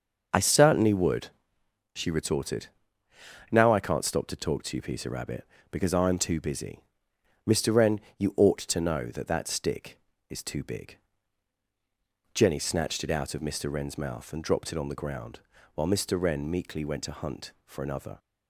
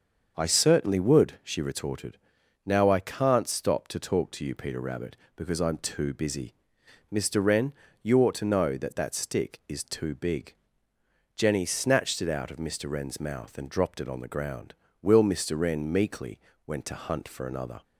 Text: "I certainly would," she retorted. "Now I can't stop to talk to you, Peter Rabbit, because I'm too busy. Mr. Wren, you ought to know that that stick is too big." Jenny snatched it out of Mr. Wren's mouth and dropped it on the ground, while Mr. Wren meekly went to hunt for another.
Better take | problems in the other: first | starts louder than the rest; until 1.3 s; 6.5 dB; noticeable in the first // says "will" for "while"; at 15.0 s // pauses between "meekly" and "went"; slight; at 16.3 s; 0.26 s long

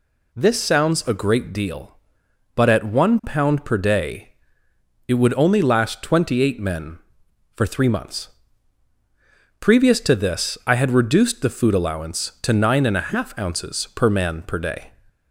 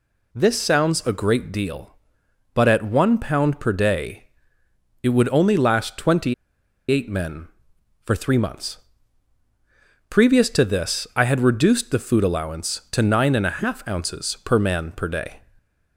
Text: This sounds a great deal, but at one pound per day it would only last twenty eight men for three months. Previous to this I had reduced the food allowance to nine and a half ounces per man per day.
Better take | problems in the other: first | pauses between "day" and "it"; noticeable; at 4.2 s; 0.74 s long; noticeable in the first // pauses between "twenty" and "eight"; noticeable; at 6.3 s; 0.56 s long

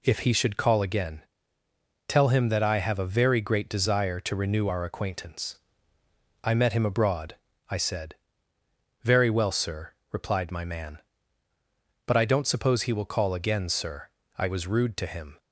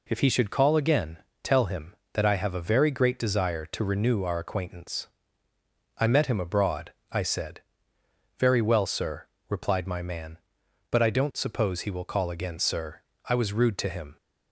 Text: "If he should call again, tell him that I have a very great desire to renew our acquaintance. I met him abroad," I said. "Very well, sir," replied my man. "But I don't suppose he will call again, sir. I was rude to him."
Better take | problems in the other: neither | none

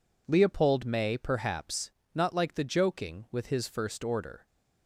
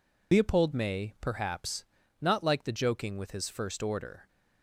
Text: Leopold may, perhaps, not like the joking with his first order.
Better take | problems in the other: first | loses the start of "Leopold"; at 0.3 s; 80 ms

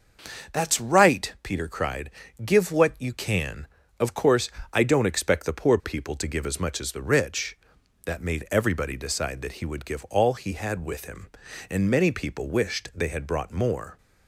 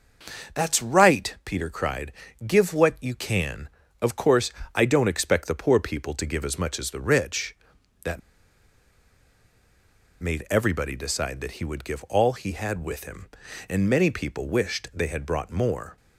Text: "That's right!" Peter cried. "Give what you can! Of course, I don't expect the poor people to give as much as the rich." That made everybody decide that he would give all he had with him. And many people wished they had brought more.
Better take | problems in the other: first | starts louder than the rest; until 1.6 s; 6.5 dB; also in the first // pauses between "That" and "made"; strong; at 8.2 s; 2.0 s long

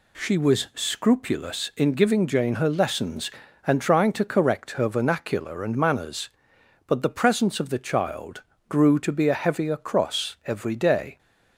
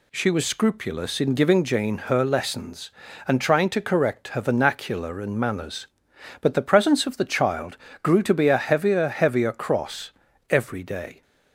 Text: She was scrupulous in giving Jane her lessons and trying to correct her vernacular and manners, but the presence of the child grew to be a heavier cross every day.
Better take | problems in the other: first | pauses between "child" and "grew"; slight; at 7.7 s; 0.24 s long; slight in the first // says "heavier" twice; at 9.0 s // pauses between "cross" and "every"; at 10.0 s; 0.40 s long

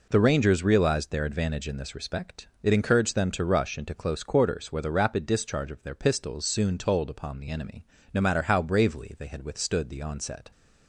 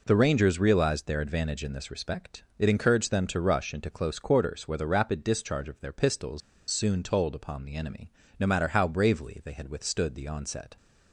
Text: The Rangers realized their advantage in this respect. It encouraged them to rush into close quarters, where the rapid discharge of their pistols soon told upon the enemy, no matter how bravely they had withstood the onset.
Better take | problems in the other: first | pauses between "pistols" and "soon"; slight; at 6.4 s; 0.30 s long

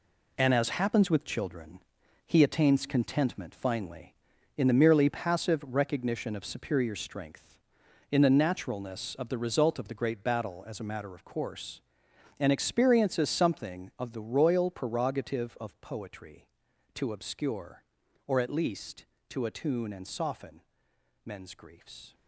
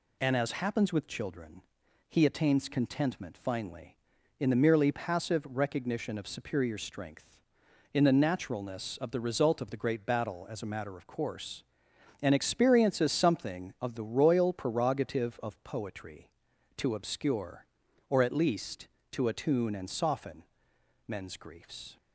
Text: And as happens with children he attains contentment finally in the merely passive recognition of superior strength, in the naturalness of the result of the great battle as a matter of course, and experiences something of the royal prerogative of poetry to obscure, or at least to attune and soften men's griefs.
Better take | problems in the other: second | gets quieter; strong; throughout; 8.5 dB // pauses between "children" and "he"; noticeable; at 1.7 s; 0.46 s long; noticeable in the second // pauses between "soften" and "men's"; noticeable; at 20.6 s; 0.64 s long; noticeable in the second

